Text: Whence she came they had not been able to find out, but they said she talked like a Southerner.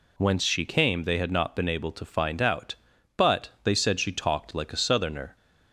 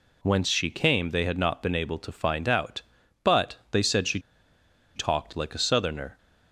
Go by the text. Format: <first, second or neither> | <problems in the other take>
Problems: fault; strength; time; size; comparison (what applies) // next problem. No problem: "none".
first | pauses between "she" and "talked"; noticeable; at 4.1 s; 0.76 s long